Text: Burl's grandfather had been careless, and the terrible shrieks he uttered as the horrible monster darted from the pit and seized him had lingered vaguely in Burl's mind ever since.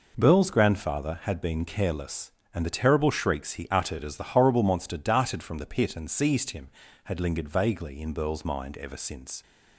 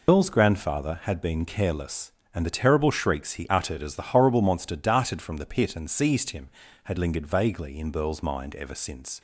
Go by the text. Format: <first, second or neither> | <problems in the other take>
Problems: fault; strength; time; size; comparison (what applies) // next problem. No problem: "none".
first | loses the start of "Burl's"; at 0.0 s; 145 ms